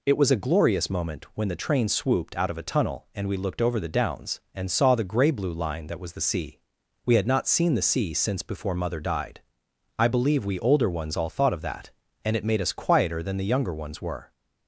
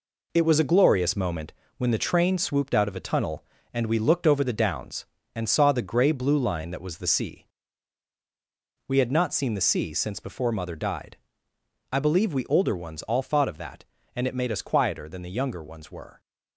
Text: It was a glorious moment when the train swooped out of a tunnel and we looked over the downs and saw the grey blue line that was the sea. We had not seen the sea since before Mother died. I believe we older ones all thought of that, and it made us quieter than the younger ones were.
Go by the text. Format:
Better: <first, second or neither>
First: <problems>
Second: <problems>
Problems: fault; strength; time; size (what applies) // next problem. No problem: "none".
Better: first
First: none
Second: gets quieter; throughout; 7 dB // pauses between "moment" and "when"; slight; at 1.5 s; 0.26 s long